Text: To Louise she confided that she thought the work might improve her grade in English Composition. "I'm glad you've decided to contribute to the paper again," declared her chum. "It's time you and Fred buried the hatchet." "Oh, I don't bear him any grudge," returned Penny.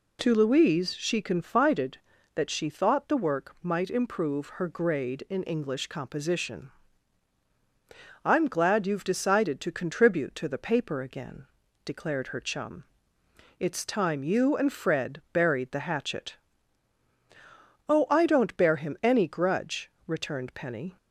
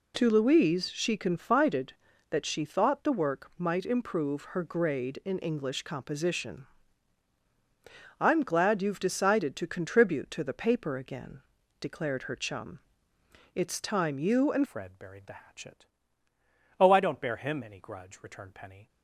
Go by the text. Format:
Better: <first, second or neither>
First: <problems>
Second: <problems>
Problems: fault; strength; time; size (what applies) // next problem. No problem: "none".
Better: first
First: none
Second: changes voice at "Fred"; from 14.6 s on; 4.2 s long